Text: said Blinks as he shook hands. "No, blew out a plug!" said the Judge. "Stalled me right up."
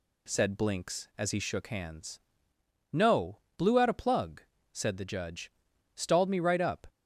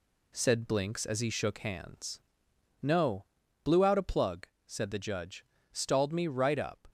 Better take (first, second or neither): first